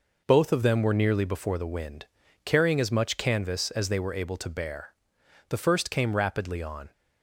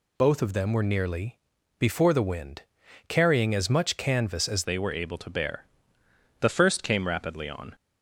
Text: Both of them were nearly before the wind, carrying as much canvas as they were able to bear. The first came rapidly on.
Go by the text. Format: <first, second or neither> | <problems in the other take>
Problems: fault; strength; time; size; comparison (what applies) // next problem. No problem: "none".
first | pauses between "nearly" and "before"; at 1.3 s; 0.40 s long // changes voice at "they"; from 4.6 s on; 3.1 s long